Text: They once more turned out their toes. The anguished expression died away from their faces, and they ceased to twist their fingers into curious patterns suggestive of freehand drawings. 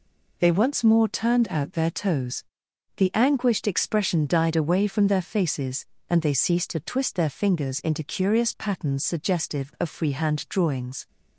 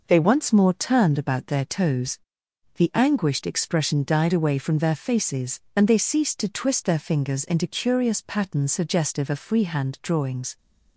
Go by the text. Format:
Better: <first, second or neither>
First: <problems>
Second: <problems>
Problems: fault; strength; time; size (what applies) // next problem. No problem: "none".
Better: first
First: none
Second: says "about" for "out"; at 1.1 s